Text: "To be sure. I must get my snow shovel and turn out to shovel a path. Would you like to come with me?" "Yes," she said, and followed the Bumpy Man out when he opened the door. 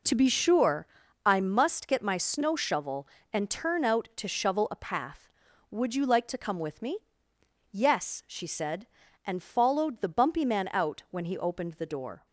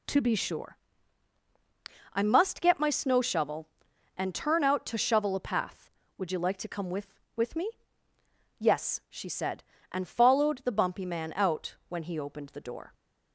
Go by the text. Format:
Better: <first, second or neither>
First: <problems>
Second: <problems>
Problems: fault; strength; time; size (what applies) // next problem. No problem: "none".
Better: first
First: none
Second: says "with" twice; at 7.3 s